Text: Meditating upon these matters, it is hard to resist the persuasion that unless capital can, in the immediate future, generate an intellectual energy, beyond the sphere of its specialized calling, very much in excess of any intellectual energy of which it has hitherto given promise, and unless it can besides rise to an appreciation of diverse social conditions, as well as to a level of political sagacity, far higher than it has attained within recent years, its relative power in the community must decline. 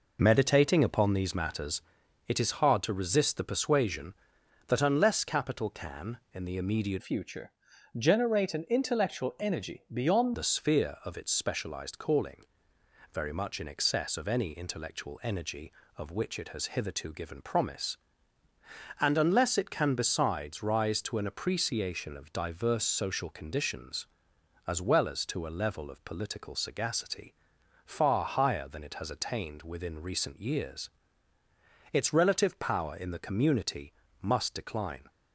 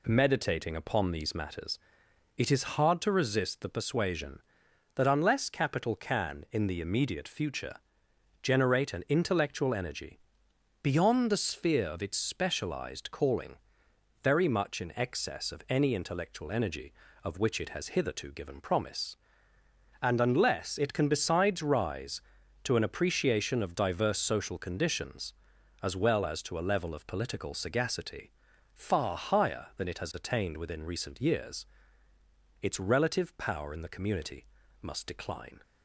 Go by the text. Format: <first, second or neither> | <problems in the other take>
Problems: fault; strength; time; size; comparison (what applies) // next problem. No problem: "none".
second | changes voice from "future" to "beyond"; from 6.9 to 10.3 s; 3.4 s long // pauses between "community" and "must"; slight; at 33.9 s; 0.28 s long; also in the second